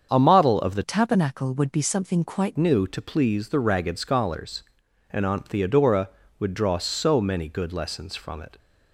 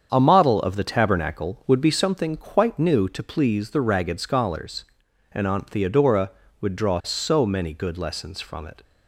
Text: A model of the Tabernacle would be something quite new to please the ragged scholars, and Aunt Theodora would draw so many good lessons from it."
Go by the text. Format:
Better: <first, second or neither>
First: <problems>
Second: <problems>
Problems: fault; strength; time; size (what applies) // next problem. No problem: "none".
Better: second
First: starts louder than the rest; strong; until 1.1 s; 7.5 dB // changes voice from "Tabernacle" to "quite"; from 0.8 to 2.5 s; 1.7 s long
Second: starts louder than the rest; strong; until 1.1 s; 7.5 dB